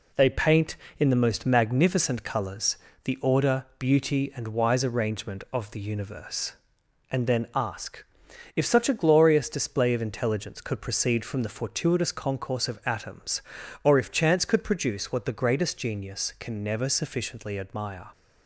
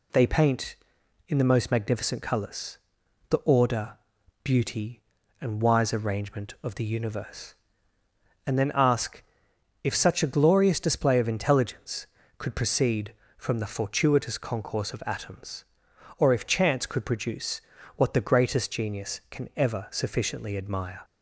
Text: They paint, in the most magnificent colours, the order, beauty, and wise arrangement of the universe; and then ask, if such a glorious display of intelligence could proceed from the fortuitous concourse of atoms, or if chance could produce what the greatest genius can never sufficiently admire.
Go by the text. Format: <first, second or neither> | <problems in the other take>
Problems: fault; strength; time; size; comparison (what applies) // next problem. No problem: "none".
first | pauses between "produce" and "what"; slight; at 17.6 s; 0.34 s long // says "ever" for "never"; at 19.5 s